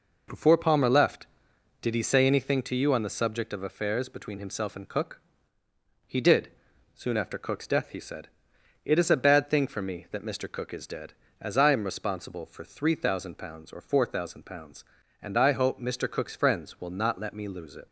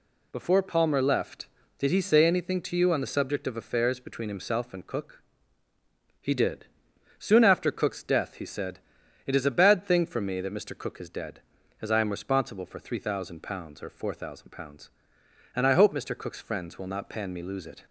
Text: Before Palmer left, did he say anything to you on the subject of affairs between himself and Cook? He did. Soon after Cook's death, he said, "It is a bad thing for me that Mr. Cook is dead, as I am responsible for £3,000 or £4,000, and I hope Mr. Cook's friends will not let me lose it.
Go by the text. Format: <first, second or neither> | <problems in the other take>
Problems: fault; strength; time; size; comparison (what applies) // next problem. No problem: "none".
first | says "pan" for "let"; at 17.0 s